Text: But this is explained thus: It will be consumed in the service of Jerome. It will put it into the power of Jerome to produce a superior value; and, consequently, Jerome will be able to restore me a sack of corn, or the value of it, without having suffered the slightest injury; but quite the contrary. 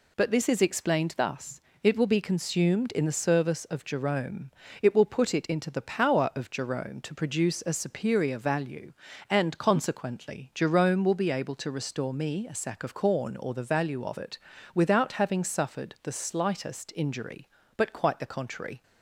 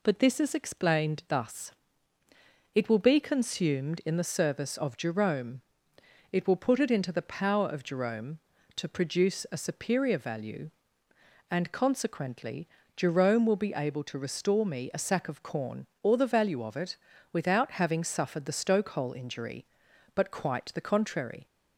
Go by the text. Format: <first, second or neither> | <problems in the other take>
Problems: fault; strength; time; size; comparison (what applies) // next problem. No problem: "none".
first | says "stokehole" for "slightest"; at 18.5 s